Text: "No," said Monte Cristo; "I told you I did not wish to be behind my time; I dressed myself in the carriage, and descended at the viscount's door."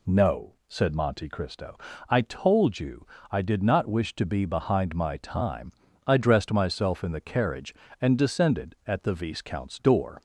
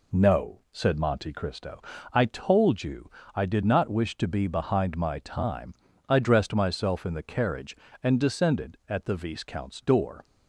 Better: first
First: pauses between "you" and "I"; slight; at 3.0 s; 0.28 s long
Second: gets quieter; noticeable; throughout; 4.5 dB // pauses between "you" and "I"; slight; at 3.0 s; 0.28 s long

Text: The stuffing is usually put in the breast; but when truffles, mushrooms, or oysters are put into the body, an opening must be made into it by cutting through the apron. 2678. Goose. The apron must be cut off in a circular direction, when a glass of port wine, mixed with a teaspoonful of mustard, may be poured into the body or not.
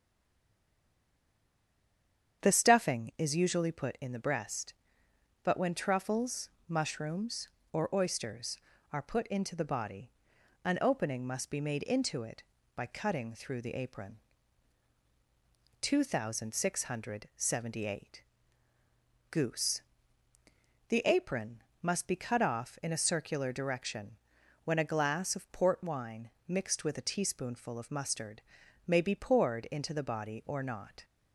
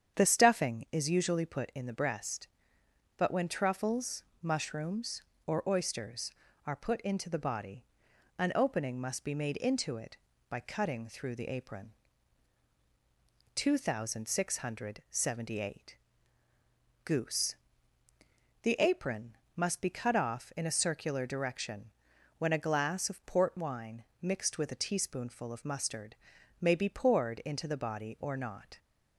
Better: second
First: stays silent before the first word; until 2.4 s; 2.4 s long // starts louder than the rest; strong; until 3.4 s; 8.5 dB // pauses between "apron" and "must"; slight; at 21.6 s; 0.20 s long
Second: starts louder than the rest; strong; until 1.2 s; 8.5 dB // pauses between "apron" and "must"; slight; at 19.3 s; 0.20 s long

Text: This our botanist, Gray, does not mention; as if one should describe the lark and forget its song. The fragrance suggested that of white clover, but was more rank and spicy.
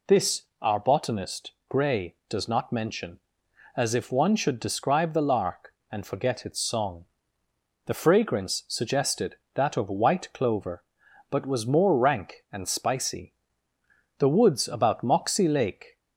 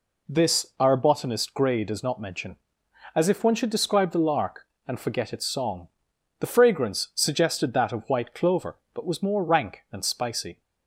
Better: second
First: pauses between "This" and "our"; slight; at 0.4 s; 0.16 s long // goes on to say "The woods about Moxie Lake"; strong; from 14.1 s on; 1.8 s long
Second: none

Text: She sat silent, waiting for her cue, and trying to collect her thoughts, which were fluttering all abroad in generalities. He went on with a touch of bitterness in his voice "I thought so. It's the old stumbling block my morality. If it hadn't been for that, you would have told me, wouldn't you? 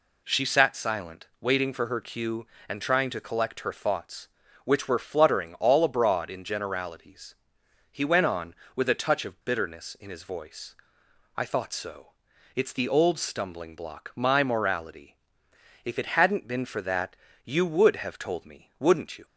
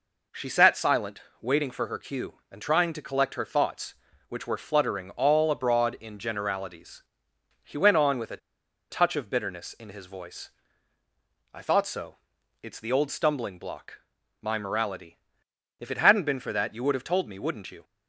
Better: first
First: pauses between "voice" and "I"; noticeable; at 10.7 s; 0.60 s long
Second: pauses between "a" and "touch"; noticeable; at 8.3 s; 0.53 s long // pauses between "voice" and "I"; at 10.4 s; 1.0 s long // pauses between "block" and "my"; at 13.9 s; 0.40 s long

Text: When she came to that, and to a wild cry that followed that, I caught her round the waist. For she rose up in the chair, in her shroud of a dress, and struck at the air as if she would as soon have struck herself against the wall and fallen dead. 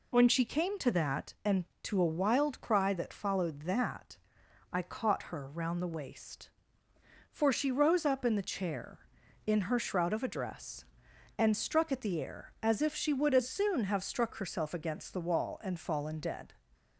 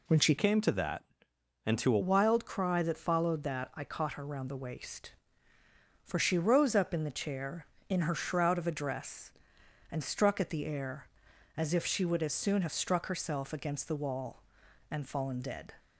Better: first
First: none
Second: changes voice from "came" to "a"; from 0.3 to 1.9 s; 1.6 s long

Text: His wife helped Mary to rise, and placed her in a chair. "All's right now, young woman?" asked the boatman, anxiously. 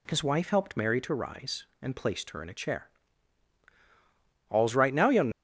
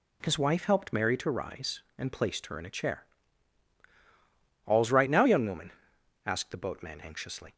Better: second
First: stops before "woman asked the boatman anxiously"; at 5.3 s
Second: none

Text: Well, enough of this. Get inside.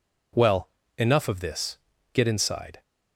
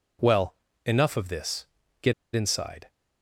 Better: first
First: none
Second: pauses between "Get" and "inside"; slight; at 2.1 s; 0.22 s long

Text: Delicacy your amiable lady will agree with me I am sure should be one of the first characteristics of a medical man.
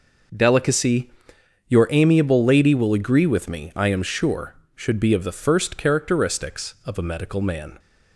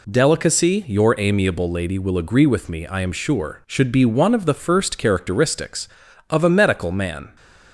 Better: second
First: pauses between "Delicacy" and "your"; noticeable; at 1.0 s; 0.60 s long // skips "one"; at 5.1 s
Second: none

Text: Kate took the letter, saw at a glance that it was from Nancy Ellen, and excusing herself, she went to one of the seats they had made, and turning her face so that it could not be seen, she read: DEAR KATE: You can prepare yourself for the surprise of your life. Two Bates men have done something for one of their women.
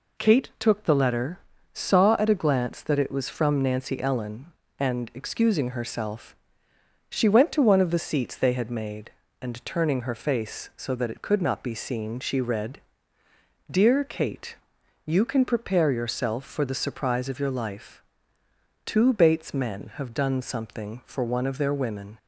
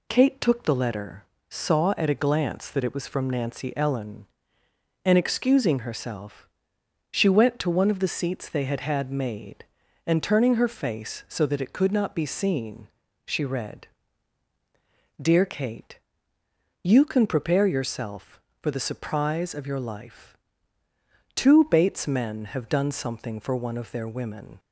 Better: first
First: none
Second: says "had" twice; at 8.8 s

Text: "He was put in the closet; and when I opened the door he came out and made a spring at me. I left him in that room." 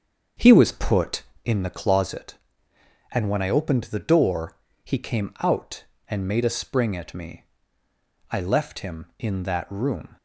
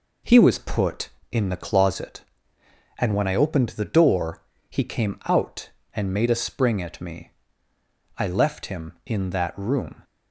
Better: second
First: starts louder than the rest; until 1.7 s; 7 dB // pauses between "door" and "he"; slight; at 4.5 s; 0.28 s long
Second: pauses between "door" and "he"; slight; at 4.4 s; 0.28 s long

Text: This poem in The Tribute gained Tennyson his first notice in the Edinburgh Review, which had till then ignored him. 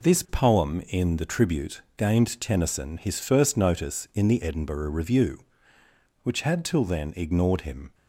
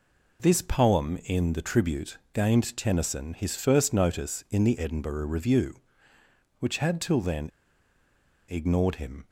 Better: first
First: pauses between "Tribute" and "gained"; slight; at 1.8 s; 0.16 s long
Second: pauses between "Tribute" and "gained"; slight; at 2.1 s; 0.16 s long // pauses between "then" and "ignored"; at 7.5 s; 1.0 s long

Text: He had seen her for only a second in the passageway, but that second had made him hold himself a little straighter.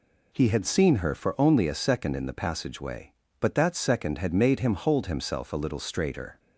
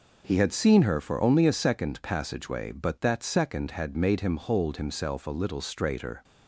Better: first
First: none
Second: skips "in the"; at 2.0 s

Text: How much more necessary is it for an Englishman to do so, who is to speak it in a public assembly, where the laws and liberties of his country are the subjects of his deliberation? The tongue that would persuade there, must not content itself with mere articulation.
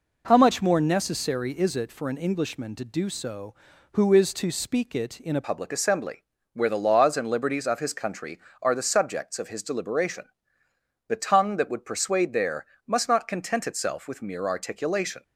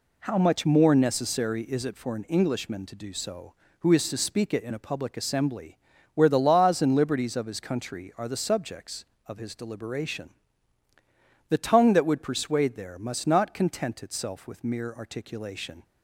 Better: second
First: changes voice at "public"; from 5.4 s on; 9.8 s long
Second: none

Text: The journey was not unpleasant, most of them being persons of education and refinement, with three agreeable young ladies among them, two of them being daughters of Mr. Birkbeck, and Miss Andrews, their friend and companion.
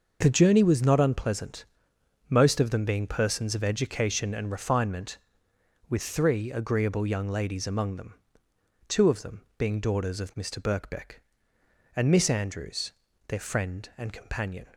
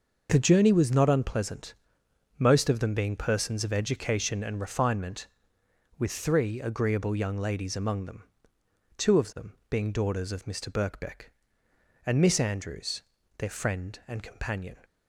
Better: neither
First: pauses between "them" and "being"; slight; at 9.4 s; 0.16 s long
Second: pauses between "them" and "being"; slight; at 9.5 s; 0.16 s long

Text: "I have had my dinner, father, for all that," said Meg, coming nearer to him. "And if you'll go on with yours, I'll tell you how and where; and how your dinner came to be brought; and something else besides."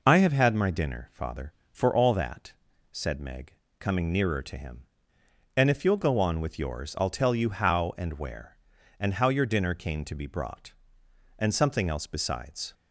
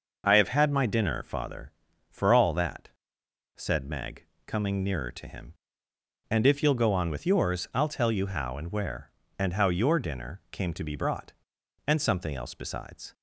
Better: neither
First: none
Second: none

